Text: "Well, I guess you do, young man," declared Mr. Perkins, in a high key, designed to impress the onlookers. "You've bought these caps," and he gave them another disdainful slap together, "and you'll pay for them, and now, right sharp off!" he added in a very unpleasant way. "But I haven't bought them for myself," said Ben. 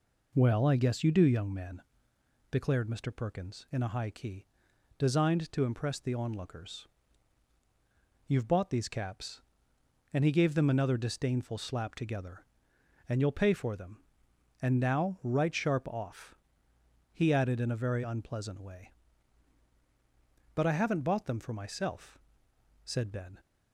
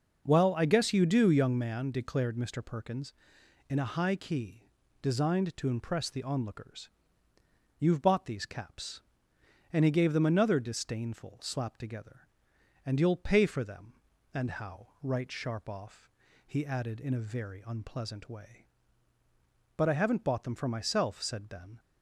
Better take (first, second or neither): first